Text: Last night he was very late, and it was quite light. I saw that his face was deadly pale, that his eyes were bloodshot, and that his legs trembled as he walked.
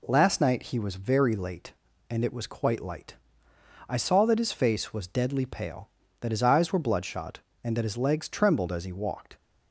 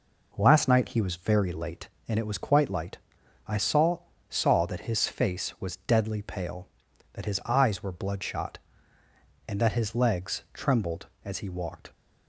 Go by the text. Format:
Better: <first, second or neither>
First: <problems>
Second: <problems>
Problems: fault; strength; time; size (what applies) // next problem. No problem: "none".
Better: first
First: none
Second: says "saw" twice; at 4.3 s